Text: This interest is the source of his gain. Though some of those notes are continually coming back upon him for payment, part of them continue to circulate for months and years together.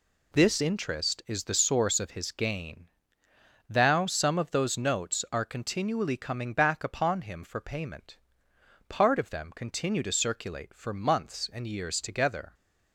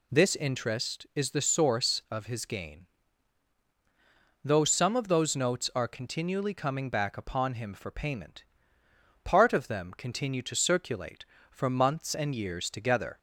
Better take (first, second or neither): second